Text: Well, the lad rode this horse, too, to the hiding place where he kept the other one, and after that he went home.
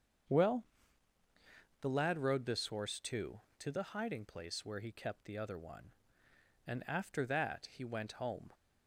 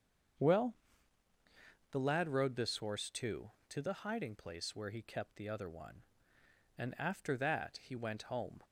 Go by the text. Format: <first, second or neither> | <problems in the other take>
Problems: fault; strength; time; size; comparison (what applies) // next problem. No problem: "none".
neither | starts louder than the rest; the same in both